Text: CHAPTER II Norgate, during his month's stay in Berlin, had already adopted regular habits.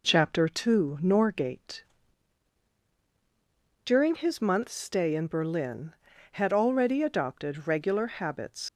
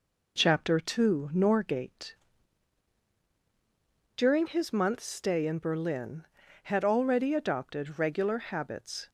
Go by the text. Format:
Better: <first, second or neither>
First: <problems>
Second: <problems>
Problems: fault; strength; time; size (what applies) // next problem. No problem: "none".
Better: second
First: leaves "habits" unfinished; at 8.6 s; 85 ms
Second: none